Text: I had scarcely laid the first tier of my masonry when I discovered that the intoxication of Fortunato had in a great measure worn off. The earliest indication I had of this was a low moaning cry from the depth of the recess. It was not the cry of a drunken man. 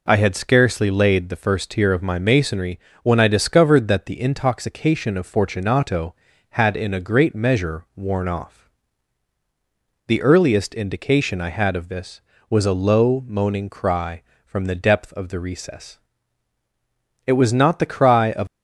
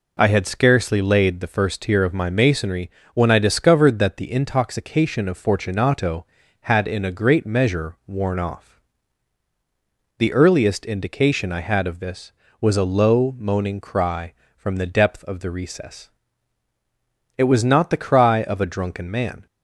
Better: second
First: pauses between "masonry" and "when"; slight; at 2.7 s; 0.24 s long // stops before "a drunken man"; at 18.4 s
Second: pauses between "masonry" and "when"; slight; at 2.9 s; 0.24 s long

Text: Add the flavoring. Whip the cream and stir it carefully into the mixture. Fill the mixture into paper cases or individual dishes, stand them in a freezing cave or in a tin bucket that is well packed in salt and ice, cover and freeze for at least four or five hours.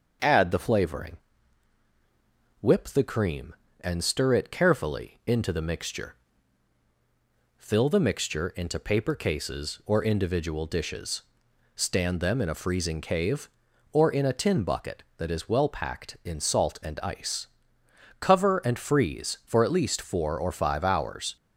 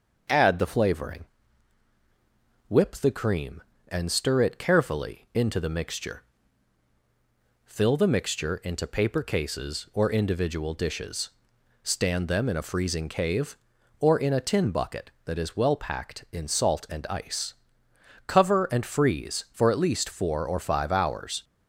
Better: neither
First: starts louder than the rest; until 2.6 s; 6 dB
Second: starts louder than the rest; until 2.7 s; 6 dB

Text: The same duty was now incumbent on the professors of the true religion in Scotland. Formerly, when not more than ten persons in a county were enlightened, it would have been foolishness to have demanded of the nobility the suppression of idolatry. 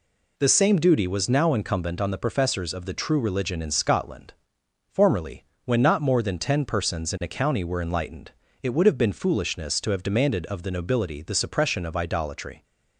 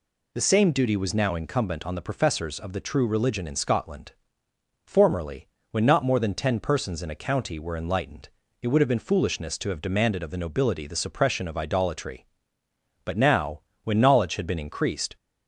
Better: first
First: none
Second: goes on to say "But now when knowledge had been increased"; strong; from 13.0 s on; 2.0 s long

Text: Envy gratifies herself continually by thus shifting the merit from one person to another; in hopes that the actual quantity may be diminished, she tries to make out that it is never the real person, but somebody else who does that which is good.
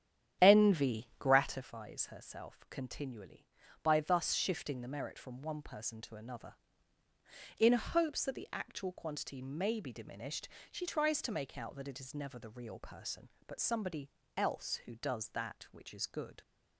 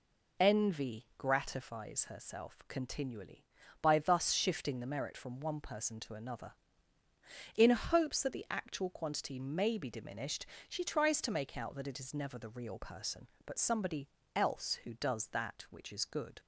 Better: second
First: starts louder than the rest; strong; until 1.6 s; 9.5 dB // pauses between "somebody" and "else"; slight; at 14.0 s; 0.26 s long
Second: pauses between "somebody" and "else"; slight; at 14.0 s; 0.26 s long

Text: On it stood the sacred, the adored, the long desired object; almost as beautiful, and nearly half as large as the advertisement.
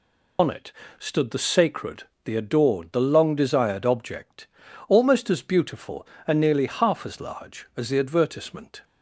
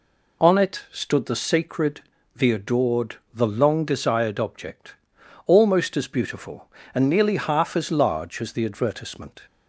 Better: second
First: loses the start of "On"; at 0.3 s; 85 ms // pauses between "it" and "stood"; slight; at 0.7 s; 0.28 s long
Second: none

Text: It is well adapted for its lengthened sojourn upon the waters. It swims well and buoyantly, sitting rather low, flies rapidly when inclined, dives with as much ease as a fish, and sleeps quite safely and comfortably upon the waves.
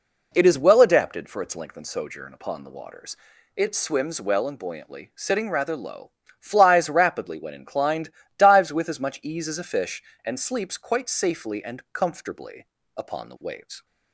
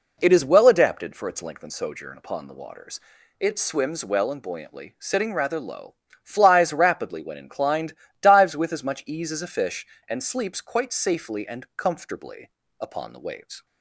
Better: neither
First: pauses between "comfortably" and "upon"; slight; at 12.6 s; 0.30 s long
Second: pauses between "comfortably" and "upon"; slight; at 12.4 s; 0.30 s long

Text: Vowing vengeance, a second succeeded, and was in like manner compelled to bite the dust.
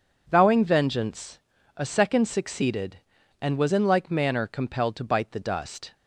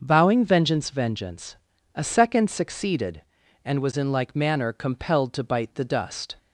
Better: first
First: none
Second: says "vengeance" twice; at 0.8 s

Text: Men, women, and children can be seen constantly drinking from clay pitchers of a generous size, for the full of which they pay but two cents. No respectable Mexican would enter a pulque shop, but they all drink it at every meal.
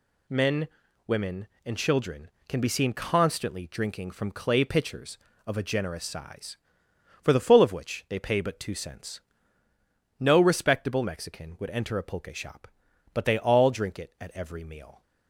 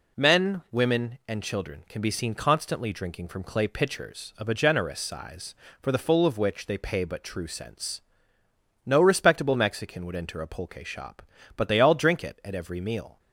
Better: first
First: none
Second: says "true" for "two"; at 7.2 s

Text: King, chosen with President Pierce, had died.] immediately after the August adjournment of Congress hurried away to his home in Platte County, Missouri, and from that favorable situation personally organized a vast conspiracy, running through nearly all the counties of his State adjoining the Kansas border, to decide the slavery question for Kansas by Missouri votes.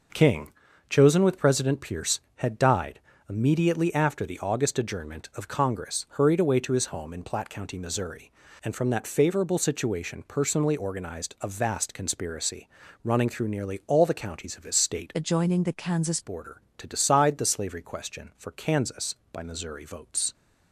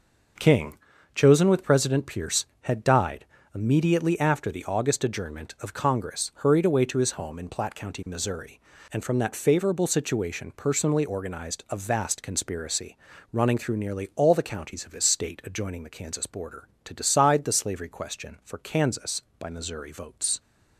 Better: second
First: changes voice from "adjoining" to "Kansas"; from 15.1 to 16.2 s; 1.1 s long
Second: none

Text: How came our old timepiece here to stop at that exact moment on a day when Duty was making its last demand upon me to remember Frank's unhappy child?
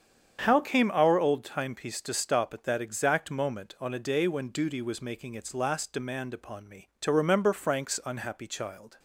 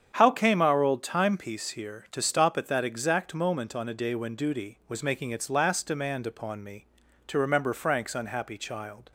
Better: second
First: starts louder than the rest; strong; until 1.4 s; 8 dB // skips "here"; at 2.0 s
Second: starts louder than the rest; strong; until 1.1 s; 8 dB

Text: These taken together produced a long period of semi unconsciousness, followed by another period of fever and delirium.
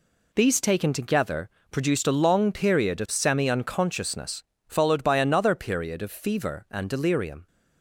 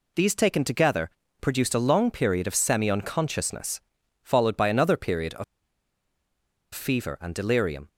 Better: first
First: pauses between "together" and "produced"; slight; at 1.5 s; 0.20 s long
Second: pauses between "together" and "produced"; slight; at 1.1 s; 0.30 s long // pauses between "of" and "fever"; strong; at 5.4 s; 1.2 s long

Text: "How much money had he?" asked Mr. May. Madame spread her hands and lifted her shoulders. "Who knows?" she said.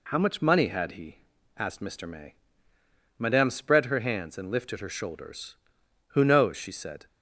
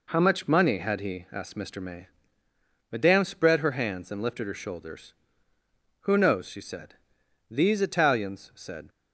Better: first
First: none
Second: goes on to say "These Italians said"; from 7.5 s on; 1.3 s long

